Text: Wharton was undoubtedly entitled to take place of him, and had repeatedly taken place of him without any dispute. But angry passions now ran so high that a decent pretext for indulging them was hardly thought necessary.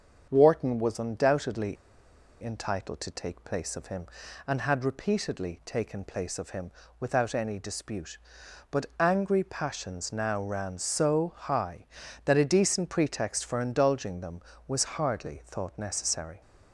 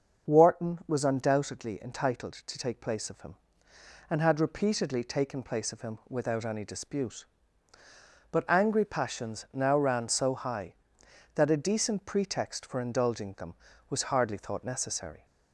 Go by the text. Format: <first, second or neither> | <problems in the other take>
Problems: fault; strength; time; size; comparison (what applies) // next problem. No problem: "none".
second | starts louder than the rest; until 1.3 s; 7 dB; also in the second // pauses between "undoubtedly" and "entitled"; noticeable; at 1.7 s; 0.67 s long // pauses between "him" and "without"; slight; at 6.7 s; 0.28 s long